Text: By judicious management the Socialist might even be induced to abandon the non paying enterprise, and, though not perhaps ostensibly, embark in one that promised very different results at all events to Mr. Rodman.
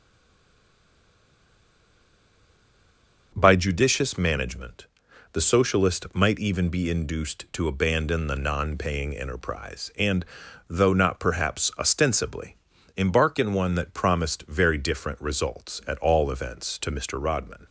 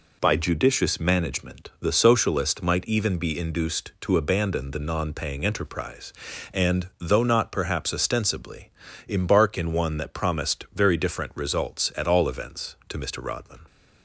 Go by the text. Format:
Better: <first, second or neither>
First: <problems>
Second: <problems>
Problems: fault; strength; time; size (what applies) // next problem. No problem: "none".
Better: second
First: stays silent before the first word; strong; until 3.3 s; 3.3 s long // pauses between "management" and "the"; noticeable; at 4.8 s; 0.46 s long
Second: none